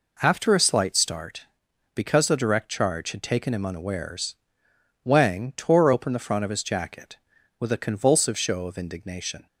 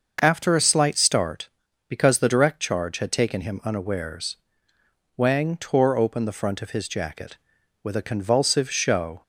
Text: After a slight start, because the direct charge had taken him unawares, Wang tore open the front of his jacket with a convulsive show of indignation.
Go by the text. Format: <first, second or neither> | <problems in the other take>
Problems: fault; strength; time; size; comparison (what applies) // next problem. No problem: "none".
first | starts louder than the rest; noticeable; until 1.2 s; 6 dB // stops before "of indignation"; at 9.2 s